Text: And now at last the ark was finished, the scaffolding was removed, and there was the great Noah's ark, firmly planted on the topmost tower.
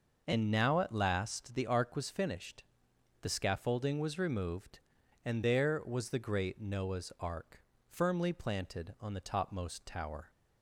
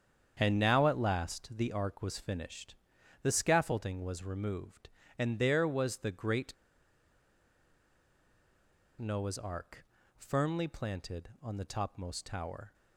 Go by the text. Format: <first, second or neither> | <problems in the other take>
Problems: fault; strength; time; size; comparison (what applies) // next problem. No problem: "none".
first | starts louder than the rest; strong; until 1.4 s; 8 dB // pauses between "great" and "Noah's"; strong; at 6.5 s; 2.4 s long